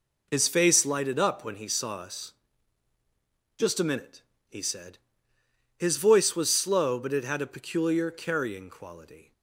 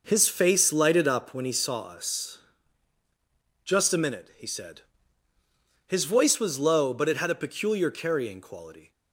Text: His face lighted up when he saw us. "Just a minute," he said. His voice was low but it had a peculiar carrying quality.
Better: second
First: says "slow" for "low"; at 6.5 s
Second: none

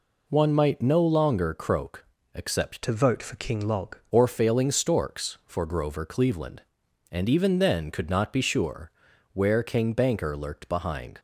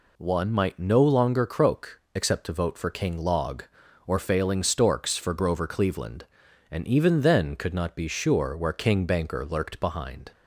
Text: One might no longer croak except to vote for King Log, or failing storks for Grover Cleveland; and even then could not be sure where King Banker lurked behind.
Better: second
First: pauses between "croak" and "except"; slight; at 2.0 s; 0.30 s long // changes voice from "to" to "Log"; from 2.8 to 3.9 s; 1.1 s long // pauses between "sure" and "where"; at 8.8 s; 0.44 s long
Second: pauses between "croak" and "except"; slight; at 1.9 s; 0.16 s long

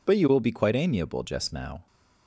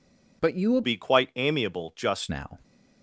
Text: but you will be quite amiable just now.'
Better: first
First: none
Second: changes voice from "be" to "just"; from 0.8 to 2.2 s; 1.4 s long

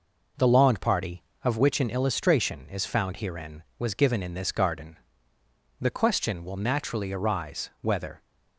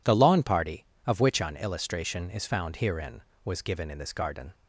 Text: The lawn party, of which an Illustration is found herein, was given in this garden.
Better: second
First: goes on to say "The question will naturally arise whether"; strong; from 5.7 s on; 2.4 s long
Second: none

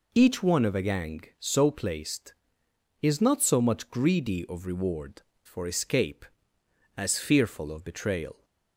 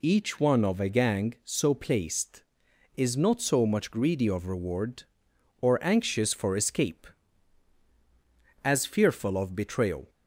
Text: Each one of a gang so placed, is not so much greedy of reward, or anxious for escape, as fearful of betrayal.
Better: second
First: skips "or anxious"; at 5.3 s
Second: none

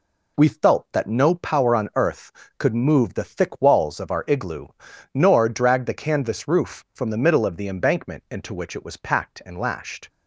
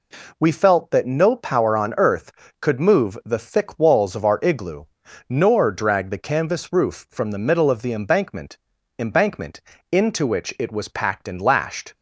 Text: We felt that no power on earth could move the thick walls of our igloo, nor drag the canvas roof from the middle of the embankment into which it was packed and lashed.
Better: first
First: none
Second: says "embankment" twice; at 8.9 s

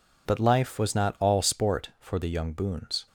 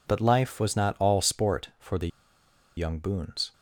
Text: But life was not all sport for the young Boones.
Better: first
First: none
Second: pauses between "the" and "young"; noticeable; at 2.0 s; 0.69 s long

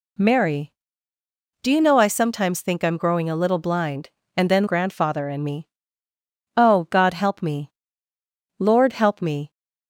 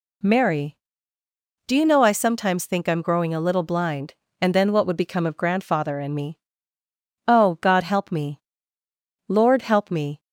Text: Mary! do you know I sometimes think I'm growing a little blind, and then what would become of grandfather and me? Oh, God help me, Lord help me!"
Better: second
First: skips "what would become of"; at 4.6 s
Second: none

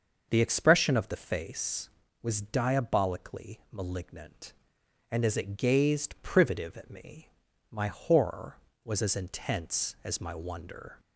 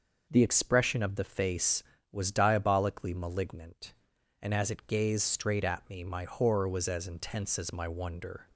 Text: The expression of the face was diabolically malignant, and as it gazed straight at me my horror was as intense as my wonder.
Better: second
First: starts louder than the rest; until 1.3 s; 6.5 dB // says "privative" for "straight"; at 6.2 s // pauses between "me" and "my"; at 7.2 s; 0.42 s long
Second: none

